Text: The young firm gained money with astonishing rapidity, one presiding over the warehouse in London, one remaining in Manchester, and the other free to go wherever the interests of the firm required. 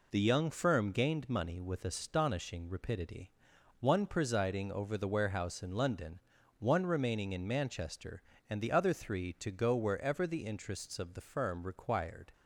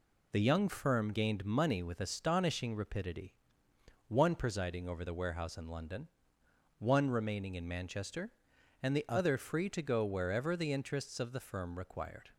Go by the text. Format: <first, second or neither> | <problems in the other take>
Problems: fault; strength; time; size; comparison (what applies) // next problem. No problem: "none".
second | says "three" for "free"; at 8.9 s